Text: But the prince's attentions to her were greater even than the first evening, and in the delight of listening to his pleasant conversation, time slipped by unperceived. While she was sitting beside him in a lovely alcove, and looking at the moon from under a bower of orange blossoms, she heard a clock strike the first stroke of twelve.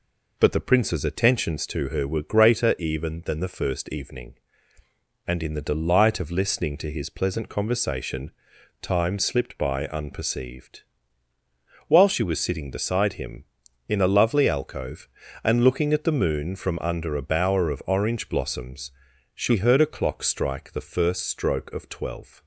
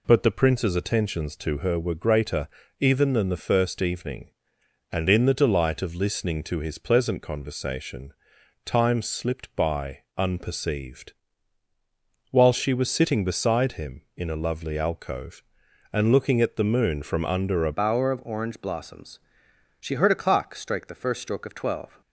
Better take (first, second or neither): first